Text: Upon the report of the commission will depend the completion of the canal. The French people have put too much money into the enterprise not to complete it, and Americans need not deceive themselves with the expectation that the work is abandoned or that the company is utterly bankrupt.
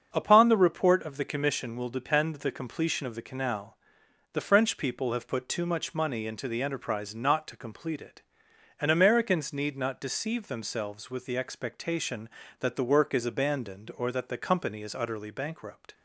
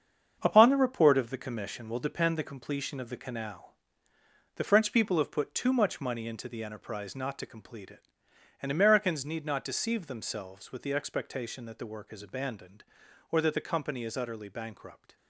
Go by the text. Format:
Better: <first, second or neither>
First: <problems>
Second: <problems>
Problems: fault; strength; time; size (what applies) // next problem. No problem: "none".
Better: first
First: starts louder than the rest; until 1.1 s; 7 dB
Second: gets quieter; strong; throughout; 8 dB // starts louder than the rest; strong; until 1.4 s; 7 dB